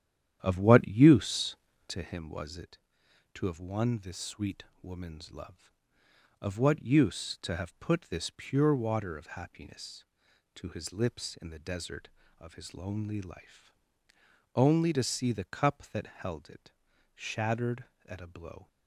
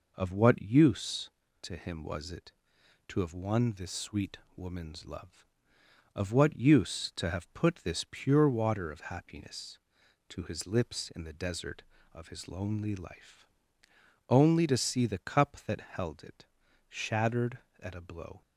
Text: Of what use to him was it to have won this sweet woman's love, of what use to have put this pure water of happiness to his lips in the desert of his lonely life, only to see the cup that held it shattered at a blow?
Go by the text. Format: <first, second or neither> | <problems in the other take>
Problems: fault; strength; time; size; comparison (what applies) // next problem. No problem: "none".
second | starts louder than the rest; strong; until 2.2 s; 10 dB // pauses between "sweet" and "woman's"; slight; at 4.6 s; 0.20 s long; slight in the second // pauses between "it" and "shattered"; at 16.7 s; 0.44 s long; also in the second